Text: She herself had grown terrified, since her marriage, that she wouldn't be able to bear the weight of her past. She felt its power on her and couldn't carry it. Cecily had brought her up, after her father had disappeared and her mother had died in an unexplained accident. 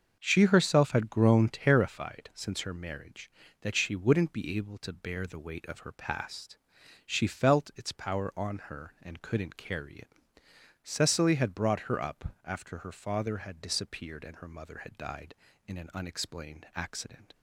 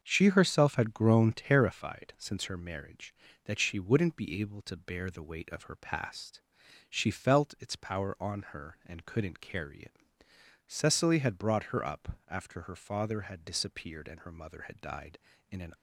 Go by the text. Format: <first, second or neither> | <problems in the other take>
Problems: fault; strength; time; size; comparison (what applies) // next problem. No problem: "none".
first | starts louder than the rest; until 1.0 s; 6.5 dB; also in the first // stops before "unexplained accident"; at 15.7 s